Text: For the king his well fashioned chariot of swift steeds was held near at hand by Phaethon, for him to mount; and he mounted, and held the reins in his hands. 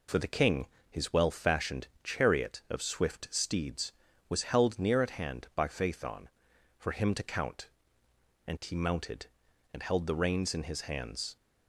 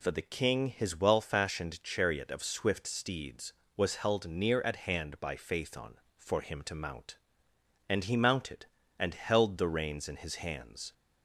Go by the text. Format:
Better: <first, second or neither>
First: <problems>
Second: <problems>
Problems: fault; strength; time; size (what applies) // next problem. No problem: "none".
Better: second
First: pauses between "king" and "his"; slight; at 0.6 s; 0.24 s long // pauses between "fashioned" and "chariot"; slight; at 1.8 s; 0.18 s long // says "count" for "mount"; at 7.2 s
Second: none